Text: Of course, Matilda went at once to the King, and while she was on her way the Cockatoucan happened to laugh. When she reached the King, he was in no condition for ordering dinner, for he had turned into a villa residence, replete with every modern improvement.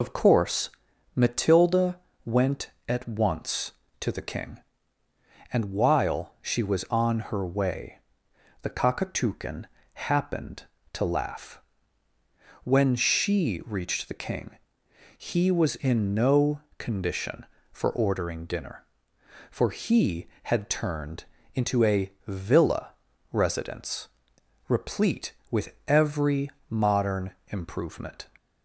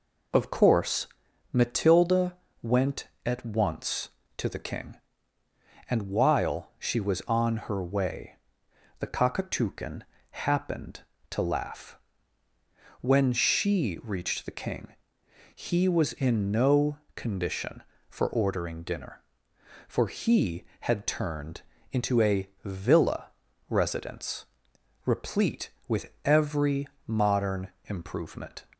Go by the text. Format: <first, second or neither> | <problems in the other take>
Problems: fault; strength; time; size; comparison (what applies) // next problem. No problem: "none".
second | loses the start of "Of"; at 0.0 s; 55 ms // pauses between "Matilda" and "went"; slight; at 1.9 s; 0.26 s long; slight in the second // pauses between "way" and "the"; noticeable; at 7.9 s; 0.62 s long; noticeable in the second // pauses between "Cockatoucan" and "happened"; slight; at 9.6 s; 0.28 s long; slight in the second // pauses between "no" and "condition"; slight; at 16.6 s; 0.18 s long; slight in the second // pauses between "turned" and "into"; slight; at 21.2 s; 0.28 s long; slight in the second // pauses between "a" and "villa"; slight; at 22.1 s; 0.16 s long; slight in the second // pauses between "villa" and "residence"; at 22.8 s; 0.42 s long; also in the second // pauses between "every" and "modern"; slight; at 26.4 s; 0.22 s long; slight in the second // pauses between "modern" and "improvement"; slight; at 27.3 s; 0.18 s long; slight in the second